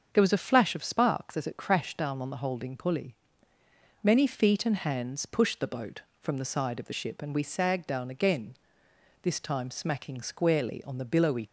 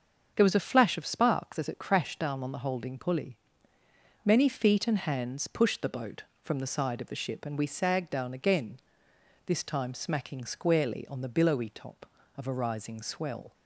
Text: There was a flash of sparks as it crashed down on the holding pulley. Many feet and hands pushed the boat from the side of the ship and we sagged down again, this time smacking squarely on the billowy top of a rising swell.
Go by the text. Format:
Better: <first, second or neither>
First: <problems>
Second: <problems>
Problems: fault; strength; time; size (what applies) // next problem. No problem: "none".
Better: second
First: starts louder than the rest; until 1.1 s; 7 dB // stops before "top of a rising swell"; at 11.4 s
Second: starts louder than the rest; until 1.3 s; 7 dB